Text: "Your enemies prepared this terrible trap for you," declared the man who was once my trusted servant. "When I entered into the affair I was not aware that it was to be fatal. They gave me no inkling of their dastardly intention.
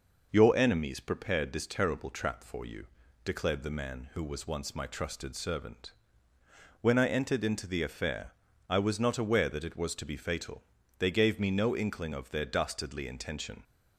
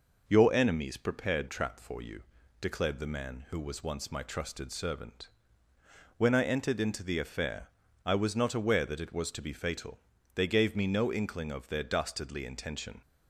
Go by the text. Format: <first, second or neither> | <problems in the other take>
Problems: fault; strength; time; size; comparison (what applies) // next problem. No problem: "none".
first | skips "this terrible"; at 1.4 s // pauses between "affair" and "I"; slight; at 7.6 s; 0.36 s long; slight in the first